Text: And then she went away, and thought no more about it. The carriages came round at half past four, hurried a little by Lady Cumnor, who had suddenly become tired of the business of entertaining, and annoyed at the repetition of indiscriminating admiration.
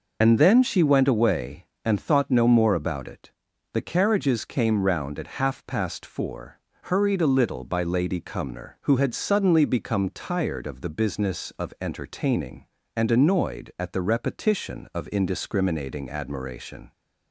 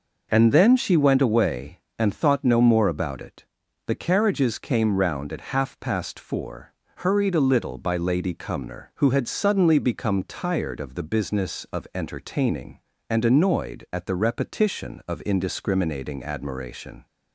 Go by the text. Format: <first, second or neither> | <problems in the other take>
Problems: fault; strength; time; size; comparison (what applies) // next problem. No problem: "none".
second | loses the start of "And"; at 0.2 s; 30 ms